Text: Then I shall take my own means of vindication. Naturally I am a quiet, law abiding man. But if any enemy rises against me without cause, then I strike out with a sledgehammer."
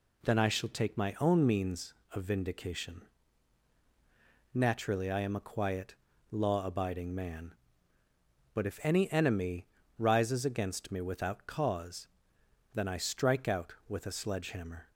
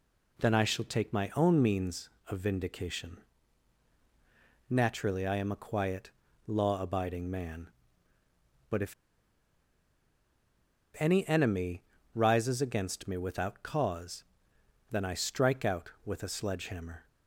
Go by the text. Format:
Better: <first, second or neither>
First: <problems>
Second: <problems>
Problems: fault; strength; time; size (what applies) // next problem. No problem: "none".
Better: first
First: pauses between "enemy" and "rises"; slight; at 9.6 s; 0.32 s long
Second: pauses between "if" and "any"; strong; at 8.9 s; 2.0 s long // pauses between "enemy" and "rises"; slight; at 11.8 s; 0.32 s long